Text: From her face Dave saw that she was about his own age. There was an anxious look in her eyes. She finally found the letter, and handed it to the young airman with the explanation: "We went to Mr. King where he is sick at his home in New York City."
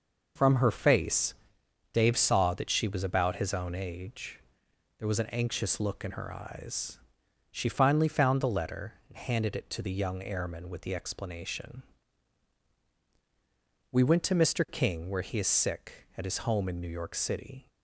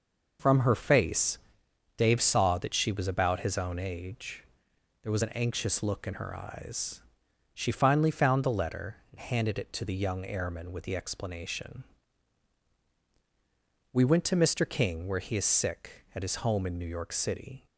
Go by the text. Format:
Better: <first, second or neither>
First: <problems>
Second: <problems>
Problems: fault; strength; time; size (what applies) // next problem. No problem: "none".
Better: neither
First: pauses between "face" and "Dave"; noticeable; at 1.3 s; 0.62 s long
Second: pauses between "face" and "Dave"; noticeable; at 1.3 s; 0.62 s long